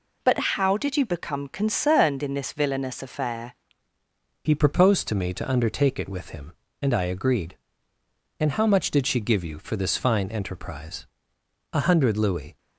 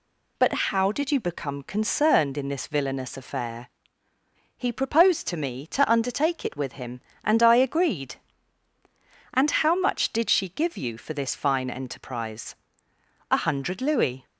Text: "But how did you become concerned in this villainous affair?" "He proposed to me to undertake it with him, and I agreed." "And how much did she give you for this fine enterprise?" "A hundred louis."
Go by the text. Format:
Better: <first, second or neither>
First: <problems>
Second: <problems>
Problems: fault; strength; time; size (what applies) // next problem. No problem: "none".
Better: second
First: pauses between "But" and "how"; slight; at 0.3 s; 0.16 s long // changes voice at "He"; from 4.4 s on; 8.1 s long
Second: pauses between "But" and "how"; slight; at 0.5 s; 0.16 s long